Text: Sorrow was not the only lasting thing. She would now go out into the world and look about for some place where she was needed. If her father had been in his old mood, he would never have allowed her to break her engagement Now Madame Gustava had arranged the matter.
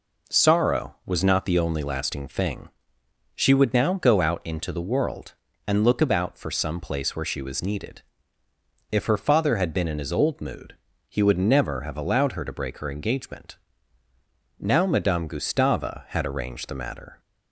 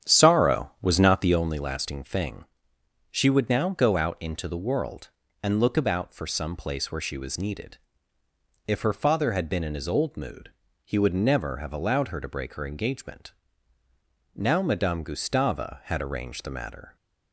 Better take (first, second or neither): first